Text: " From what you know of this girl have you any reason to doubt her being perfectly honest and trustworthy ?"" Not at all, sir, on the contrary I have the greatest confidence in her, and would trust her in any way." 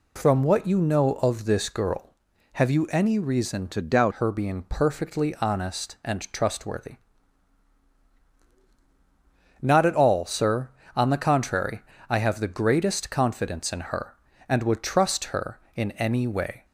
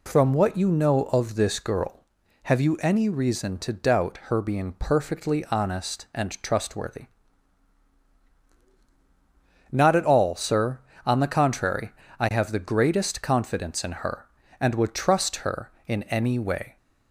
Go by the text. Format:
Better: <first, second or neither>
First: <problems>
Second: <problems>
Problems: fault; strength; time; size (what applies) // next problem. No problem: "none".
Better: second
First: changes voice from "to" to "doubt"; from 3.7 to 4.1 s; 0.4 s long // pauses between "contrary" and "I"; slight; at 11.8 s; 0.30 s long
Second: pauses between "contrary" and "I"; slight; at 11.9 s; 0.30 s long